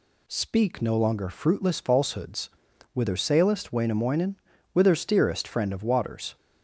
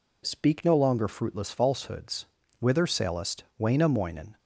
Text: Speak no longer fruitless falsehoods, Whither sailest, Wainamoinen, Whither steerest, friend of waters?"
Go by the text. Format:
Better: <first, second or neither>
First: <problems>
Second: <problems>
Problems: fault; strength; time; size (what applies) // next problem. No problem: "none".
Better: first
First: none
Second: stops before "Whither steerest friend of waters"; at 4.3 s